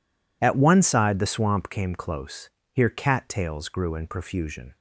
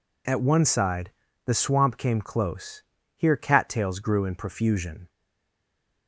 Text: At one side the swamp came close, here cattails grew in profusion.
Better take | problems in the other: first | pauses between "side" and "the"; slight; at 1.1 s; 0.34 s long // stays silent after the last word; from 5.0 s on; 1.0 s long

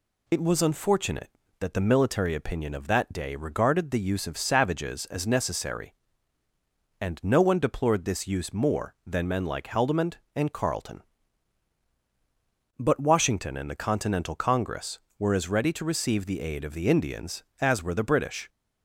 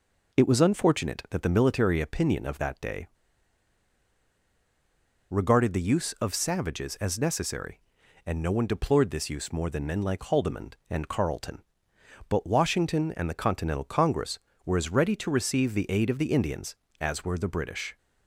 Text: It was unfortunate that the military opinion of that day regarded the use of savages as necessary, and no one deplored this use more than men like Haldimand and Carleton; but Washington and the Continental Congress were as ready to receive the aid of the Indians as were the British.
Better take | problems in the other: first | pauses between "day" and "regarded"; strong; at 3.0 s; 2.2 s long

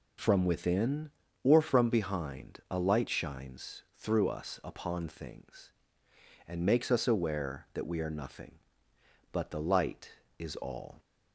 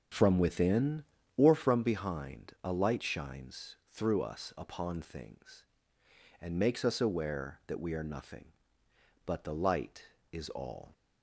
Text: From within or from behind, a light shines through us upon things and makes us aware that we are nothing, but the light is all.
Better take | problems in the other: first | starts louder than the rest; strong; until 1.7 s; 8 dB

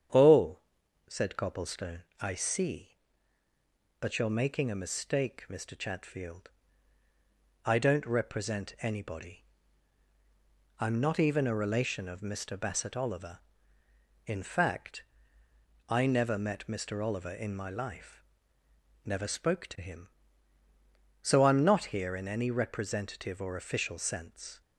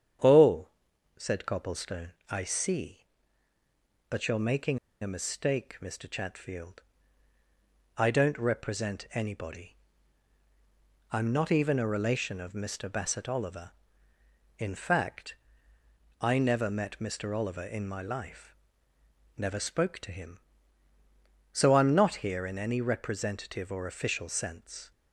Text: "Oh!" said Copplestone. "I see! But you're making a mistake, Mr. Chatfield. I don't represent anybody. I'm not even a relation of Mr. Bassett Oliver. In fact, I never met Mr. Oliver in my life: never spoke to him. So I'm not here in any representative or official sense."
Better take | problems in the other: first | starts louder than the rest; strong; until 1.7 s; 8.5 dB; strong in the first // pauses between "making" and "a"; slight; at 4.7 s; 0.23 s long

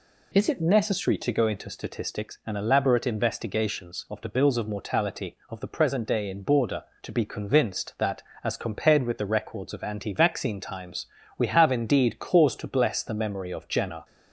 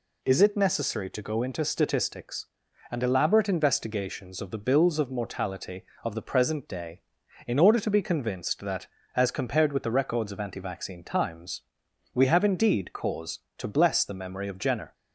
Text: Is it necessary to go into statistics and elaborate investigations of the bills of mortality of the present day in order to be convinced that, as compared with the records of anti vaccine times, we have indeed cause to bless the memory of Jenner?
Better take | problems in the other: second | says "border" for "order"; at 6.4 s

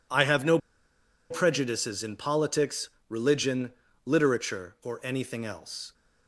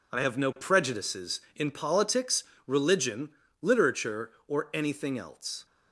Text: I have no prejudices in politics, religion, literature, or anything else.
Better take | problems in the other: second | pauses between "no" and "prejudices"; noticeable; at 0.5 s; 0.71 s long

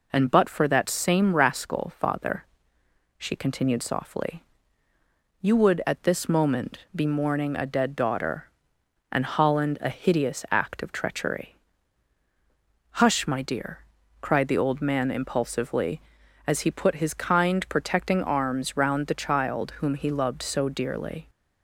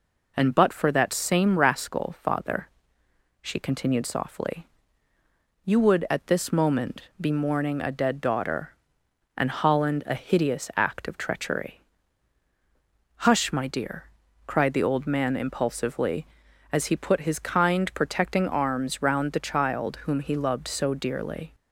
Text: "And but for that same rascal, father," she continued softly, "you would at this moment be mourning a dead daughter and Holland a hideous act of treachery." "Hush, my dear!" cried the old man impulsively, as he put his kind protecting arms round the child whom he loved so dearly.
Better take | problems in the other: neither | none

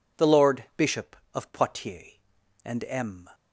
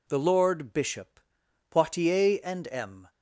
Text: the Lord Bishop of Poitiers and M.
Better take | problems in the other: first | skips "of"; at 1.4 s

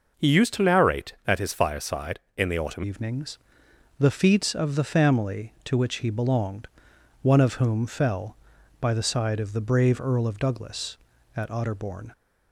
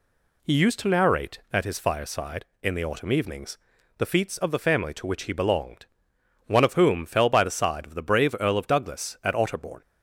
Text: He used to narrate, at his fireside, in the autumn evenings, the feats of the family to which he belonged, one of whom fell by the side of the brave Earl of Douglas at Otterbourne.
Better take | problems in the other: second | changes voice at "evenings"; from 2.8 s on; 9.3 s long

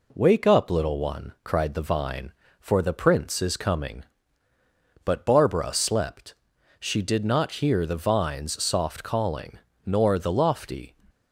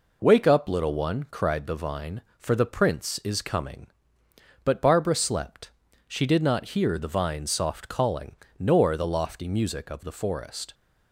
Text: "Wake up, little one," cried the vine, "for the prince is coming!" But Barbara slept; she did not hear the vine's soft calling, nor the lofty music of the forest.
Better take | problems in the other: second | stops before "music of the forest"; at 11.0 s

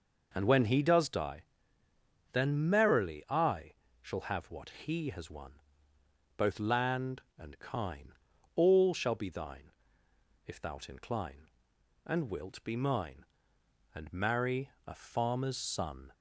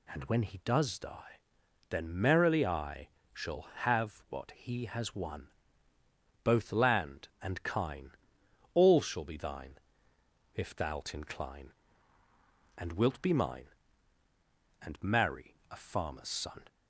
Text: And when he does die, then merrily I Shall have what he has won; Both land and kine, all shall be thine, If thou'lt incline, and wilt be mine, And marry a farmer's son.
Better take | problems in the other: neither | pauses between "I" and "Shall"; slight; the same in both // pauses between "marry" and "a"; slight; the same in both

